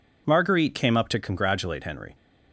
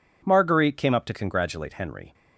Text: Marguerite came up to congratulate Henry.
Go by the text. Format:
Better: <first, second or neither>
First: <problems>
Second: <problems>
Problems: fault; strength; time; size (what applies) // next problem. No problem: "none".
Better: neither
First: none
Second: none